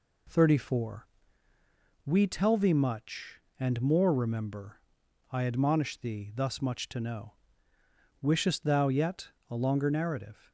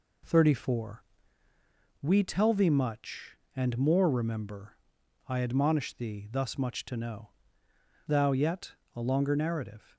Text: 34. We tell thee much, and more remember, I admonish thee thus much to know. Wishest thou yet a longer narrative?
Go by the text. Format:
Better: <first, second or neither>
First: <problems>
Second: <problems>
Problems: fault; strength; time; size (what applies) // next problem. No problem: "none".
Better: first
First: pauses between "yet" and "a"; slight; at 9.2 s; 0.18 s long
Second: skips "Wishest"; at 7.6 s // pauses between "yet" and "a"; slight; at 8.7 s; 0.20 s long